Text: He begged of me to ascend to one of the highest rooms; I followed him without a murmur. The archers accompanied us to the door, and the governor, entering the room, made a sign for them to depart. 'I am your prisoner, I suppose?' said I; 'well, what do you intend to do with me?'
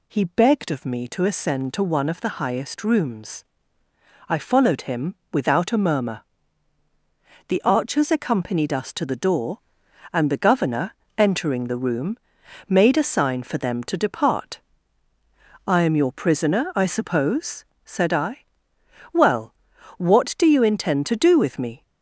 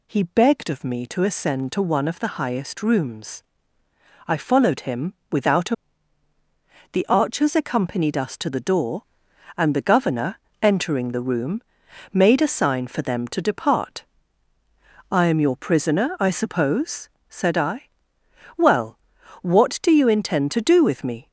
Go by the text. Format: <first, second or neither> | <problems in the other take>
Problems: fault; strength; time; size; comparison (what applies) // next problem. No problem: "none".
first | pauses between "him" and "without"; slight; at 5.1 s; 0.18 s long; slight in the first // skips "murmur"; at 6.3 s